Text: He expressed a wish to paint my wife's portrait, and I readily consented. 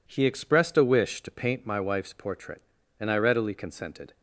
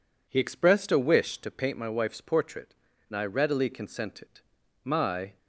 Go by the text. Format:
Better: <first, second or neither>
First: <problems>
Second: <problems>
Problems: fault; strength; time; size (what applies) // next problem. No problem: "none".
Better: first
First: none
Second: goes on to say "My"; from 4.8 s on; 0.54 s long